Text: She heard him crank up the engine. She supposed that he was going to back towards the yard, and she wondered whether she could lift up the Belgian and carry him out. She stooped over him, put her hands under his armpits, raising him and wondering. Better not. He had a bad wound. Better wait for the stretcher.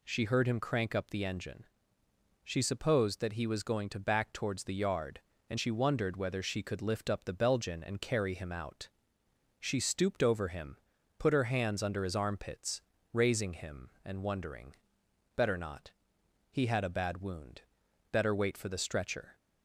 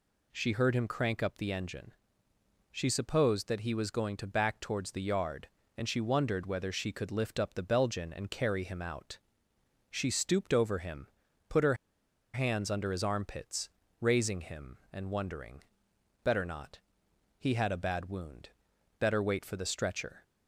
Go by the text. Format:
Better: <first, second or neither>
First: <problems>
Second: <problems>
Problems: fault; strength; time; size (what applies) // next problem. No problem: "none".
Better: first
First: none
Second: pauses between "her" and "hands"; noticeable; at 11.7 s; 0.59 s long